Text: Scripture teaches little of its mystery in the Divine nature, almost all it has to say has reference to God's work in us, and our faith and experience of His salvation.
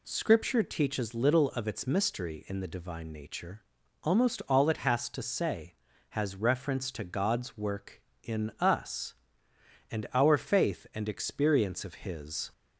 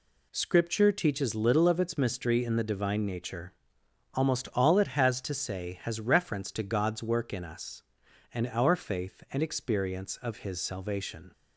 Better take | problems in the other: second | stops before "salvation"; at 12.5 s

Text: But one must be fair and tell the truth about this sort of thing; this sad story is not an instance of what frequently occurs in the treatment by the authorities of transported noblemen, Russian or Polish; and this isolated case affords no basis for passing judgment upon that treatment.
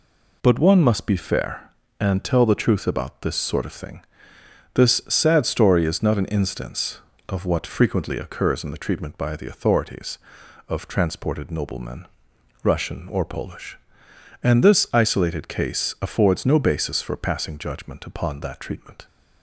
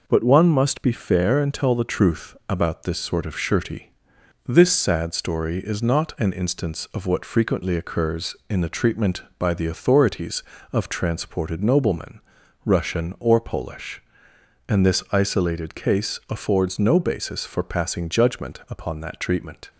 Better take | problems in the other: first | says "shirty" for "thing"; at 3.3 s

